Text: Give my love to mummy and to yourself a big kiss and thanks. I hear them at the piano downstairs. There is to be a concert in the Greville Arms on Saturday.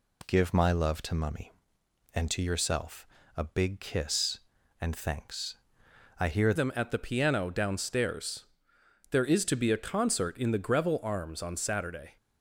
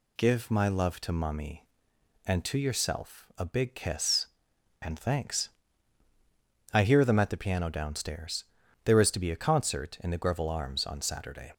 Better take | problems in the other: second | pauses between "yourself" and "a"; slight; at 3.0 s; 0.30 s long // changes voice at "them"; from 6.5 s on; 5.6 s long

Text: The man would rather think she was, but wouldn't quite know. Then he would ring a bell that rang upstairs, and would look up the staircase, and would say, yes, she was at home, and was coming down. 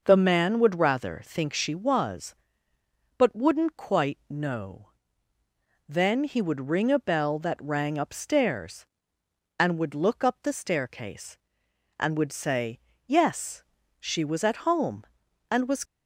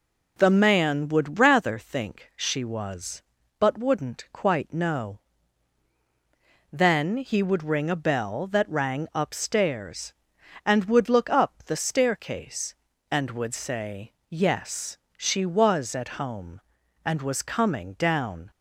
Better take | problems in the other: second | stops before "coming down"; at 15.8 s

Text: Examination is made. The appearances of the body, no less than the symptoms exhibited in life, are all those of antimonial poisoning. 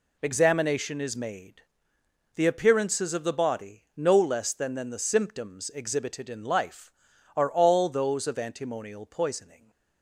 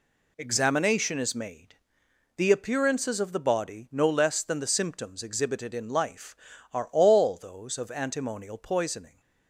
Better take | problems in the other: second | says "than" twice; at 4.7 s

